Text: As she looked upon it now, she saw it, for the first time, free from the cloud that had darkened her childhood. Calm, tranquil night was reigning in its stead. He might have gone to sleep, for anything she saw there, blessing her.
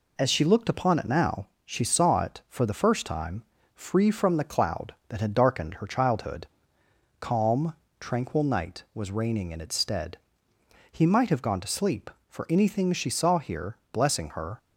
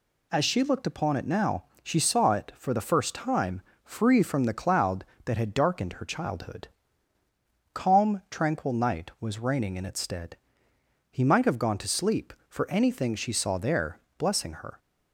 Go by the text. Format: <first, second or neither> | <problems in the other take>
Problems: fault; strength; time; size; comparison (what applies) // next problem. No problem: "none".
second | says "here" for "there"; at 13.3 s